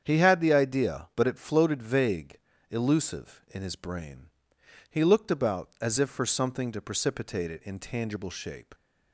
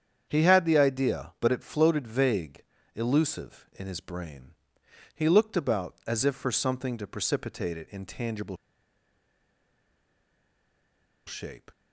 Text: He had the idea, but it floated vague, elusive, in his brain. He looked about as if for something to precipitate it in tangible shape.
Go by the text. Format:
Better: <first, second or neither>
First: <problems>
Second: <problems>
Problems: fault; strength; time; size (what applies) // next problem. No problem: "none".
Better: first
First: starts louder than the rest; strong; until 1.0 s; 8 dB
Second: starts louder than the rest; strong; until 1.2 s; 8 dB // pauses between "tangible" and "shape"; strong; at 8.5 s; 2.7 s long